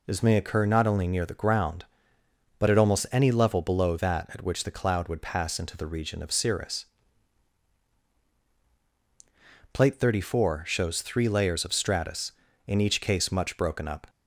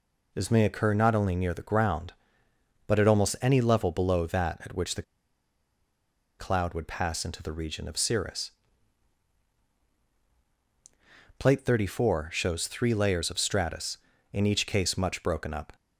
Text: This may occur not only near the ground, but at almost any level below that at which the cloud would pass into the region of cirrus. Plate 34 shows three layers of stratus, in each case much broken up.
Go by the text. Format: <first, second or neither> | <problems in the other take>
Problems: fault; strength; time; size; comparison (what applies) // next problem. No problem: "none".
first | pauses between "the" and "cloud"; strong; at 5.0 s; 1.3 s long